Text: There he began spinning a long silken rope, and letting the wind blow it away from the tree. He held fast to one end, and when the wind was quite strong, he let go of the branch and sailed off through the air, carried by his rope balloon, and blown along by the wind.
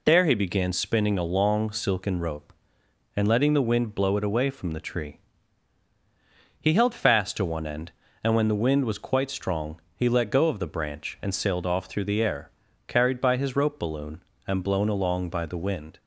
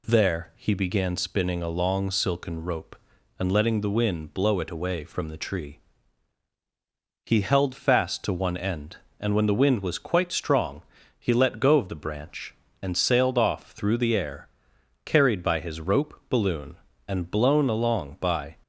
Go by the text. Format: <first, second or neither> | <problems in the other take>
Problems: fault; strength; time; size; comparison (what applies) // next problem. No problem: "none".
first | stops before "the wind"; at 18.6 s